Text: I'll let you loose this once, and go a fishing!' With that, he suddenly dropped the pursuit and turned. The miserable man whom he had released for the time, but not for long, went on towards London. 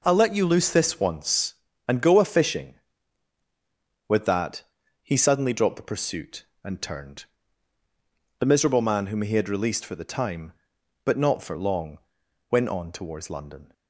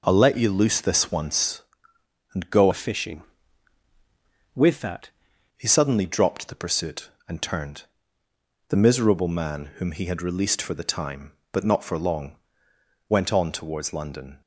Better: first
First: none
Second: changes voice from "a" to "that"; from 2.7 to 5.0 s; 2.3 s long

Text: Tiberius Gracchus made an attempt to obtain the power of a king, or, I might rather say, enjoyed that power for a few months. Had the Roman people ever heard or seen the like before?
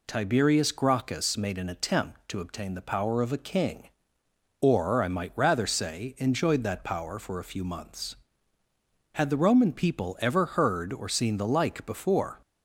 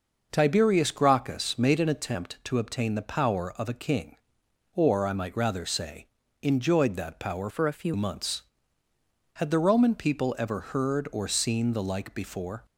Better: first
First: none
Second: changes voice from "for" to "few"; from 7.4 to 7.9 s; 0.5 s long

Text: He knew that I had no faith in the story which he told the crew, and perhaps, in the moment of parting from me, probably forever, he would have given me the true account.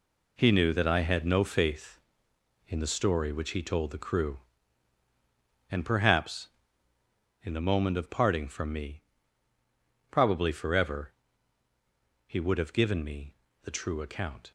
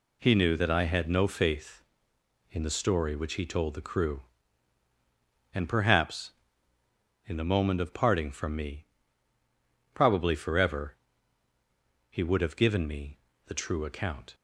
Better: second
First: gets quieter; strong; throughout; 9 dB // pauses between "me" and "the"; slight; at 13.3 s; 0.28 s long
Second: pauses between "me" and "the"; slight; at 13.1 s; 0.28 s long

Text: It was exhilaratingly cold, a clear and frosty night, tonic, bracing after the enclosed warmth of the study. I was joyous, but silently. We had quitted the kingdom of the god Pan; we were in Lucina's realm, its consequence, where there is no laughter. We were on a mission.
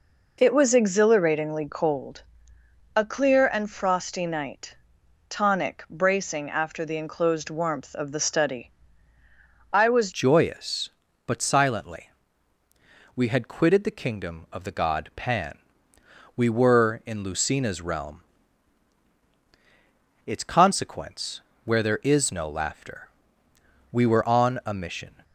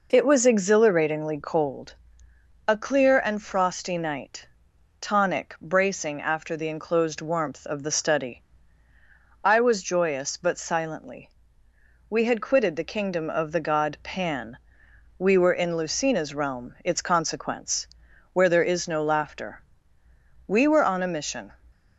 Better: second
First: changes voice at "joyous"; from 10.1 s on; 15.1 s long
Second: none

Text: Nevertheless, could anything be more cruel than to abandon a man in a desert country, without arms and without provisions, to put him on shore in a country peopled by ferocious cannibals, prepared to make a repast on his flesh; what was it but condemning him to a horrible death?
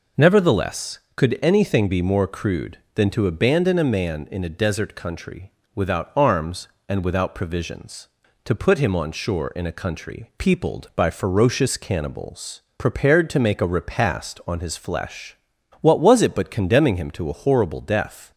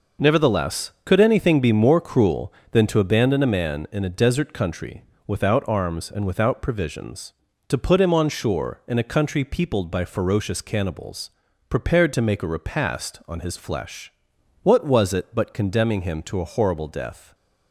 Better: second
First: says "crude" for "cruel"; at 2.2 s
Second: none

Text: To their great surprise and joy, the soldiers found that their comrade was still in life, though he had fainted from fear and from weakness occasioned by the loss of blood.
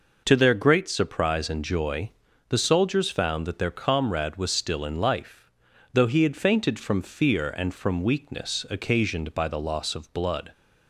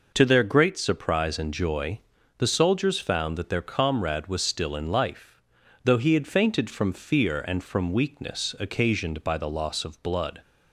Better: neither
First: none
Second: none

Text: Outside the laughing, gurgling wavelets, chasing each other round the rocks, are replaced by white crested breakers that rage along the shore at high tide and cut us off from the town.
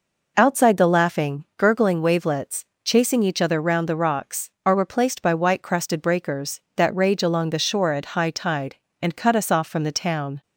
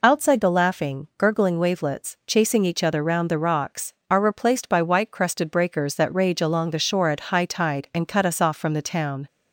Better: neither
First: none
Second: none

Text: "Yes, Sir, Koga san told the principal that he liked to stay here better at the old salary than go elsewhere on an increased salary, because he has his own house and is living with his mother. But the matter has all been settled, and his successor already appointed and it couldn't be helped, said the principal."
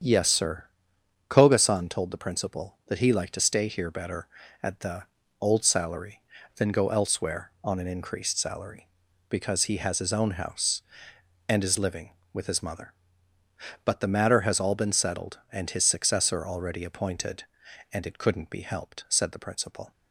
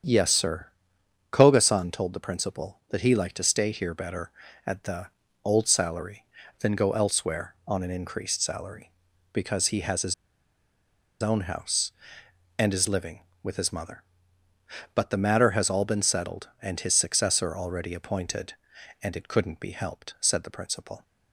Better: first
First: starts louder than the rest; strong; until 1.6 s; 8 dB // pauses between "the" and "old"; slight; at 5.0 s; 0.36 s long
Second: starts louder than the rest; strong; until 1.7 s; 8 dB // pauses between "the" and "old"; slight; at 5.0 s; 0.36 s long // pauses between "his" and "own"; at 10.1 s; 1.0 s long

